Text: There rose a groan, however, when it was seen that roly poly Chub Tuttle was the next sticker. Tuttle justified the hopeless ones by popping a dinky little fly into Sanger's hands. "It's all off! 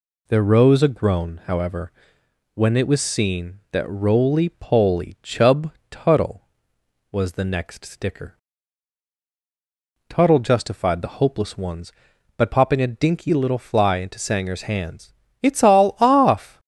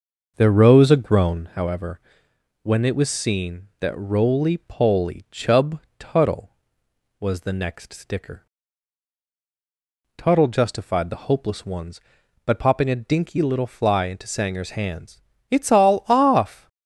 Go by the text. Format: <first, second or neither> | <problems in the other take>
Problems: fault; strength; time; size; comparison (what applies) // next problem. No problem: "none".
first | starts louder than the rest; noticeable; until 1.5 s; 6 dB // pauses between "Chub" and "Tuttle"; slight; at 5.7 s; 0.20 s long; slight in the first